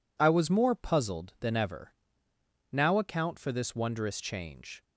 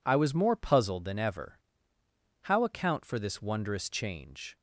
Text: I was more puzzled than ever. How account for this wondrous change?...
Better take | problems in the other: second | says "Now" for "How"; at 2.7 s

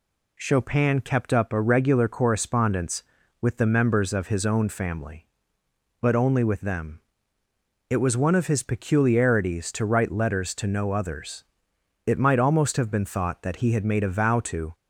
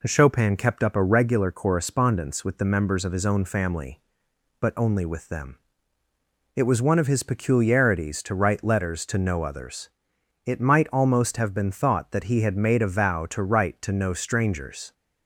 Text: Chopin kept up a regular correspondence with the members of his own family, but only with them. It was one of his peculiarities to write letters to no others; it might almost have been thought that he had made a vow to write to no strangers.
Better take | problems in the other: second | stops before "write to no strangers"; at 14.7 s

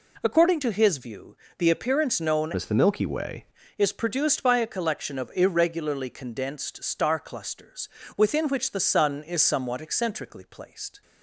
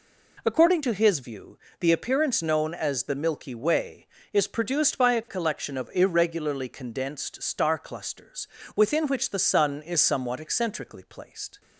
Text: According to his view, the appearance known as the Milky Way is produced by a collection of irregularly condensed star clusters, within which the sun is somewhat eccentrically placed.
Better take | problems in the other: second | changes voice from "as" to "Way"; from 2.5 to 3.4 s; 0.9 s long

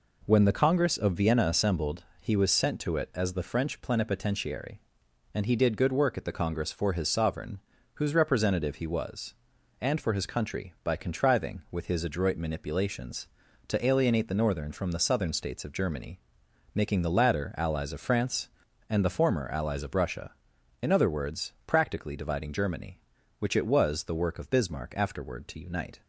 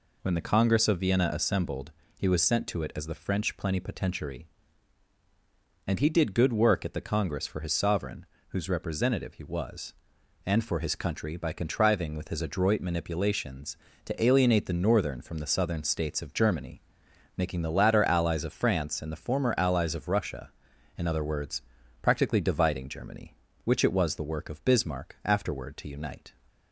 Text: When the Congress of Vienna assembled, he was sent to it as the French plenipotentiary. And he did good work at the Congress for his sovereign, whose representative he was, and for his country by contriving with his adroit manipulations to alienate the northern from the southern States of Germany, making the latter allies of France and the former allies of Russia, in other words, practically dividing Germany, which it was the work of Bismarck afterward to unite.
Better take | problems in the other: neither | none

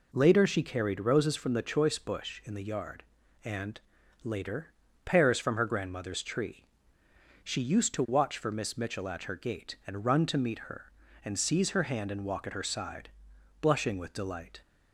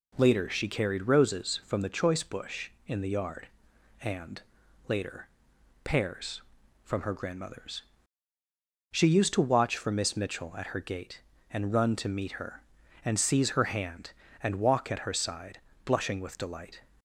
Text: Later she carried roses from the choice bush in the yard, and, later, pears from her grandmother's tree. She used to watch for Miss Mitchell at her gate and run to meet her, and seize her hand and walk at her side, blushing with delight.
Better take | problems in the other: first | skips "tree"; at 8.3 s

